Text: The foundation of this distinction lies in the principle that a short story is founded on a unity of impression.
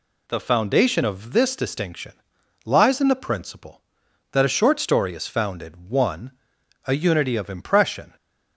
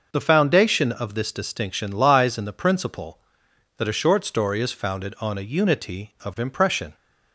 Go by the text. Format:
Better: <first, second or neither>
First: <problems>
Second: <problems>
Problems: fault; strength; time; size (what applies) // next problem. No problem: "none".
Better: second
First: pauses between "distinction" and "lies"; noticeable; at 2.1 s; 0.52 s long // says "one" for "on"; at 5.8 s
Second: none